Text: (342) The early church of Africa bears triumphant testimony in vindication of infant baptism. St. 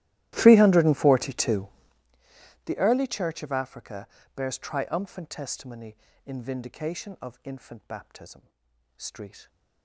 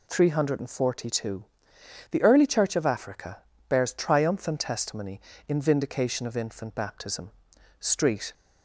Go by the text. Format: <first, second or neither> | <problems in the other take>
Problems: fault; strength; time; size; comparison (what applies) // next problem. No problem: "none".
second | starts louder than the rest; strong; until 2.1 s; 15.5 dB // pauses between "Africa" and "bears"; slight; at 4.0 s; 0.26 s long; slight in the second